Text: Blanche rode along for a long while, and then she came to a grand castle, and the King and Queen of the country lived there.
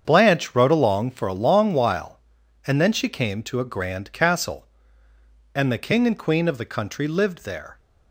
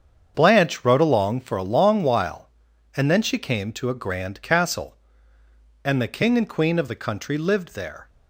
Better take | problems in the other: neither | starts louder than the rest; strong; the same in both

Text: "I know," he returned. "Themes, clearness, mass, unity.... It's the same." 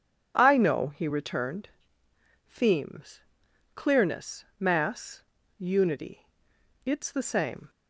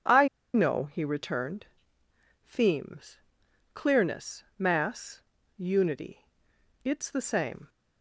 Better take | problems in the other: first | pauses between "I" and "know"; slight; at 0.2 s; 0.26 s long

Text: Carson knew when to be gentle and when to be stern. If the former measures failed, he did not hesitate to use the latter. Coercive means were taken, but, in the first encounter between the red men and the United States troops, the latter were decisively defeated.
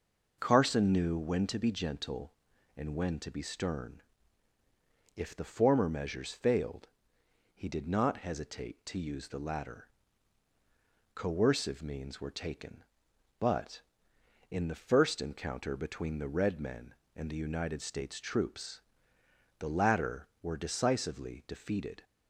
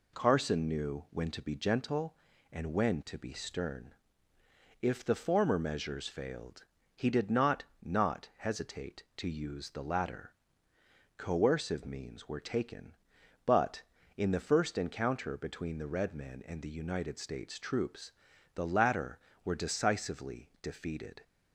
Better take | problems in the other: first | says "not" twice; at 7.8 s

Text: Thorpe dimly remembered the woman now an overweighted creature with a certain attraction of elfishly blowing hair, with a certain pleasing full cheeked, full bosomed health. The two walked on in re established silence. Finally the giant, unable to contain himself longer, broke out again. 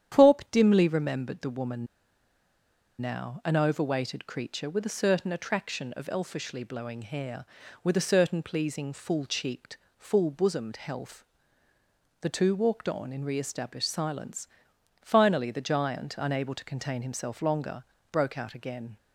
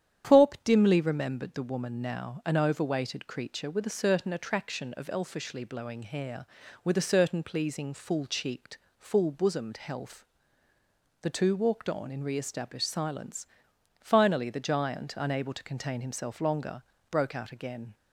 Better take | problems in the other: second | starts louder than the rest; strong; until 1.2 s; 9.5 dB; strong in the second // pauses between "woman" and "now"; at 1.8 s; 1.1 s long

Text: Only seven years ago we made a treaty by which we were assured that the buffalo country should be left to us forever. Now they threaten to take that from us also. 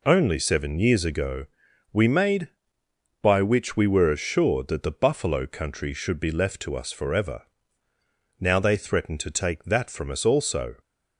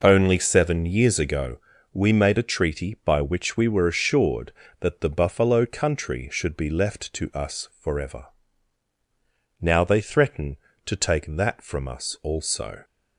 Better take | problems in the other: second | pauses between "ago" and "we"; noticeable; at 1.4 s; 0.46 s long; slight in the second // skips "a treaty"; at 2.8 s

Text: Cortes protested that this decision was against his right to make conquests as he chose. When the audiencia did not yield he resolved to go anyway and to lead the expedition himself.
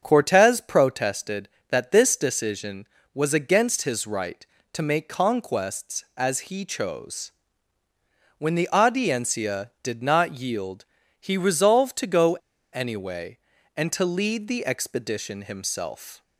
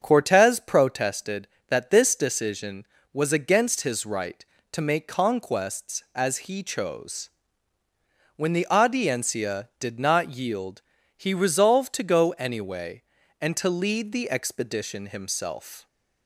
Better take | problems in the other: second | starts louder than the rest; until 1.1 s; 7 dB; also in the second // pauses between "yield" and "he"; at 10.8 s; 0.38 s long; also in the second // pauses between "go" and "anyway"; at 12.3 s; 0.40 s long

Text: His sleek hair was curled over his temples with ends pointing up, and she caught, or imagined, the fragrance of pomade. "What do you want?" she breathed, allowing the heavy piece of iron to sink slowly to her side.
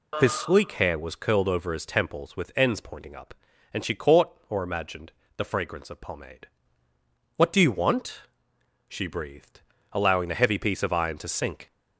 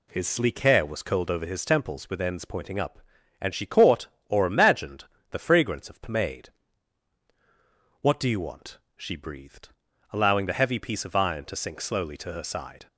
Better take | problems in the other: second | stops before "slowly to her side"; at 11.7 s

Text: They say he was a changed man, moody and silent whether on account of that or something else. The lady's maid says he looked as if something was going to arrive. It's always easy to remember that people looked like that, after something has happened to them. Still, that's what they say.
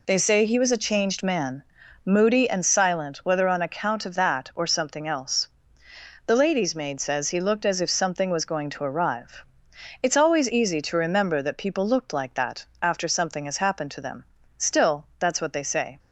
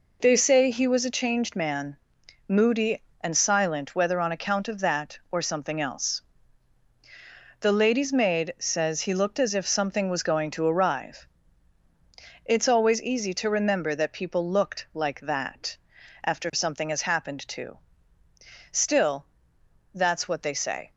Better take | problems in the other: first | skips "them"; at 18.2 s

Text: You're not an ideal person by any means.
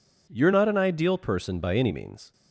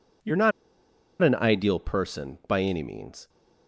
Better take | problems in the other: first | pauses between "not" and "an"; noticeable; at 0.5 s; 0.71 s long

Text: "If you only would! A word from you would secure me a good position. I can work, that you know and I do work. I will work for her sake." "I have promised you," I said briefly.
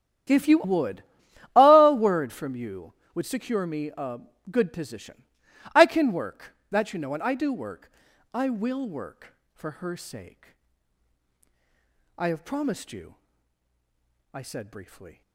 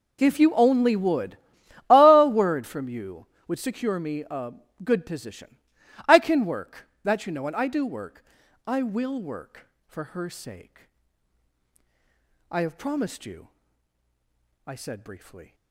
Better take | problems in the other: second | starts louder than the rest; strong; until 1.8 s; 10.5 dB // skips "only"; at 0.6 s // pauses between "a" and "good"; slight; at 4.1 s; 0.30 s long; slight in the second

